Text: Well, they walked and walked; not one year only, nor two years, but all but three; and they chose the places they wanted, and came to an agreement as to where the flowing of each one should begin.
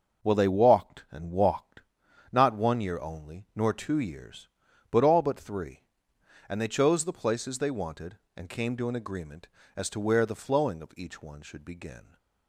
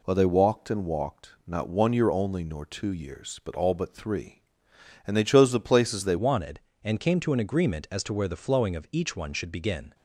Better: first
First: none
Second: changes voice at "wanted"; from 6.1 s on; 3.8 s long

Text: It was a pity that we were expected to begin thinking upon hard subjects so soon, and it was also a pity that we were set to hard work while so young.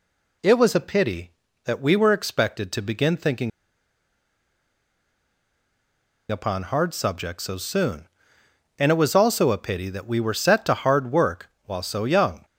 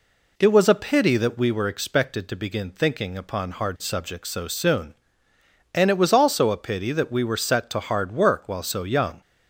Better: second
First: pauses between "thinking" and "upon"; strong; at 3.5 s; 2.8 s long // pauses between "work" and "while"; slight; at 11.4 s; 0.16 s long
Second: none

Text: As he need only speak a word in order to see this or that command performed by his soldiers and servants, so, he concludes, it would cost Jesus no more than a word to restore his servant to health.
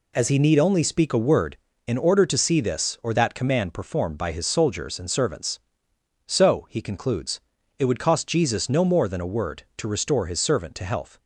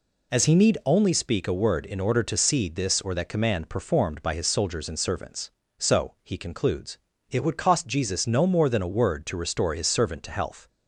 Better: neither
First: none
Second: none

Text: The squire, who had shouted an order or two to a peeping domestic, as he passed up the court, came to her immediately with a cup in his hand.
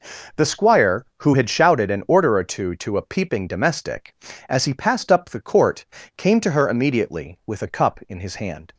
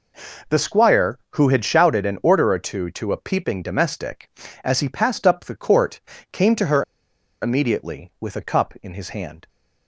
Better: first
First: none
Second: pauses between "her" and "immediately"; noticeable; at 6.8 s; 0.57 s long

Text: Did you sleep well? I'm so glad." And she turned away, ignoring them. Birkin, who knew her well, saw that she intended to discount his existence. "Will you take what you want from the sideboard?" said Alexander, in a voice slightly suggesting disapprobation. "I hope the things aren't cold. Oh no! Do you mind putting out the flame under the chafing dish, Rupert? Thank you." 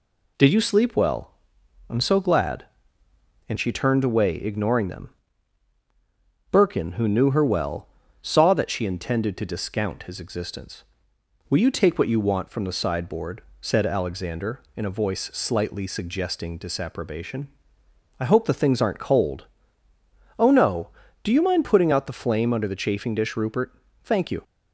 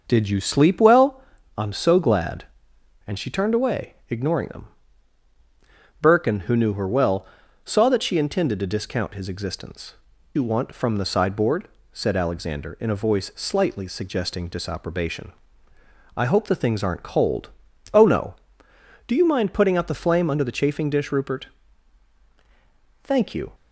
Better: first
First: none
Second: starts louder than the rest; noticeable; until 1.0 s; 6 dB // skips "Will you take what"; at 10.1 s

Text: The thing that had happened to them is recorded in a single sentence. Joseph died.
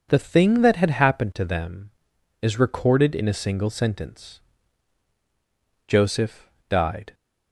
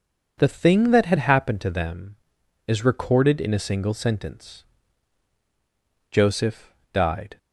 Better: neither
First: pauses between "Joseph" and "died"; slight; at 6.4 s; 0.18 s long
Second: pauses between "Joseph" and "died"; slight; at 6.7 s; 0.18 s long

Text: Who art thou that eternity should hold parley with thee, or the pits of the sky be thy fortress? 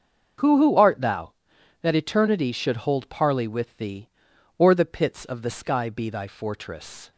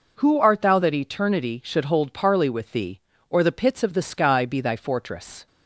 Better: second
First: starts louder than the rest; until 1.8 s; 7 dB // says "Who" twice; at 0.5 s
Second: none

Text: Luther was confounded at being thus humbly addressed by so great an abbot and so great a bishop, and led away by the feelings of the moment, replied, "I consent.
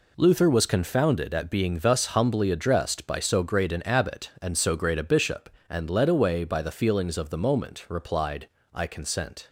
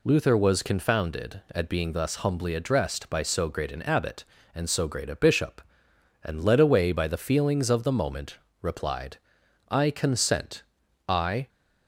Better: first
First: none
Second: goes on to say "I"; slight; from 11.0 s on; 0.42 s long

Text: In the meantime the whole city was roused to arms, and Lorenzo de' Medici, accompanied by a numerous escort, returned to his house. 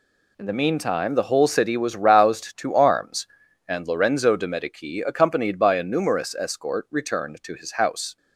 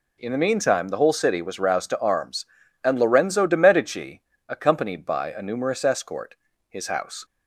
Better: first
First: none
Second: skips "returned to"; at 6.5 s

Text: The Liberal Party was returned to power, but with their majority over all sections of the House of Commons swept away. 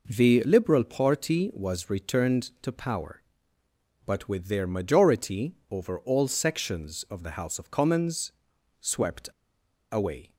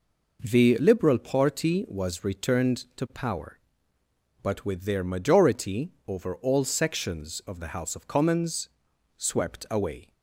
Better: second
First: pauses between "Commons" and "swept"; noticeable; at 8.3 s; 0.50 s long // pauses between "swept" and "away"; noticeable; at 9.2 s; 0.64 s long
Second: pauses between "Commons" and "swept"; noticeable; at 8.6 s; 0.50 s long

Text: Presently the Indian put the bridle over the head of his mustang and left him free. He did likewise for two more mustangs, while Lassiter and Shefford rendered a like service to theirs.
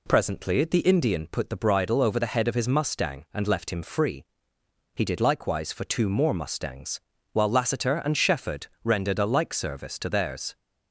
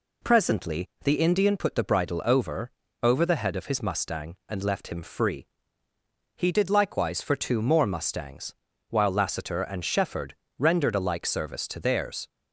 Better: first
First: pauses between "Shefford" and "rendered"; slight; at 8.6 s; 0.18 s long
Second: pauses between "Presently" and "the"; slight; at 0.8 s; 0.16 s long // says "over" twice; at 3.0 s // pauses between "Shefford" and "rendered"; slight; at 10.3 s; 0.24 s long

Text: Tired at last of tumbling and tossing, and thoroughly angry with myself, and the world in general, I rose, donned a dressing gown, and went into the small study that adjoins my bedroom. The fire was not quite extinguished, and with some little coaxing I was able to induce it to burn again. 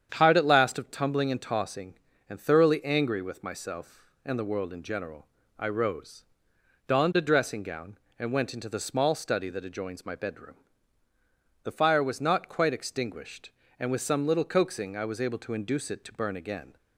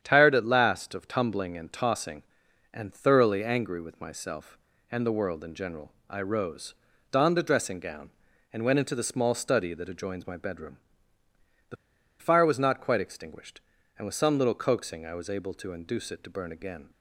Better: first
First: starts louder than the rest; strong; until 1.1 s; 8.5 dB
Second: starts louder than the rest; strong; until 1.0 s; 9 dB // pauses between "The" and "fire"; at 11.7 s; 0.44 s long

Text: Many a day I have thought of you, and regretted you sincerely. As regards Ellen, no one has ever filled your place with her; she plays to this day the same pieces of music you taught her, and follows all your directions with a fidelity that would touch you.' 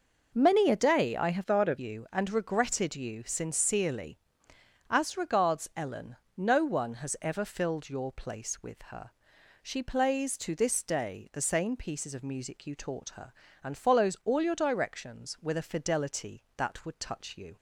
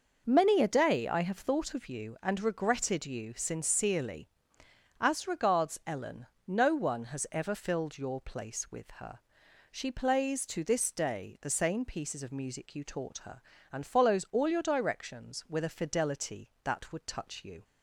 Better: second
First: changes voice from "thought" to "of"; from 1.4 to 1.7 s; 0.3 s long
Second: none

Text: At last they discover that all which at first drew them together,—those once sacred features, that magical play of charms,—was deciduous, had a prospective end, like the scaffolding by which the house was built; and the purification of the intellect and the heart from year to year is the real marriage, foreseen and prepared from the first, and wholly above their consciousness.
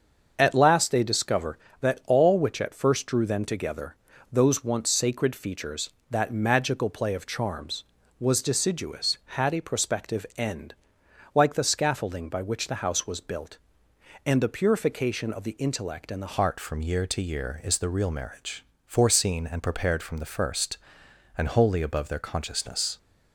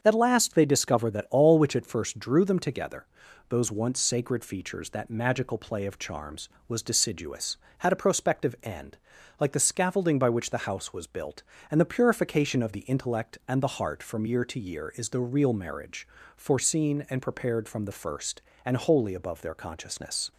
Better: second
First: starts louder than the rest; until 1.3 s; 7 dB // changes voice at "heart"; from 16.3 s on; 6.6 s long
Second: starts louder than the rest; strong; until 1.0 s; 7 dB

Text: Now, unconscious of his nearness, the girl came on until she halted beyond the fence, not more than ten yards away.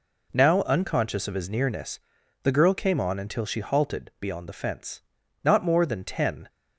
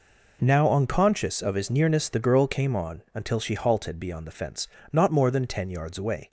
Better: second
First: stops before "yards away"; at 6.4 s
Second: none

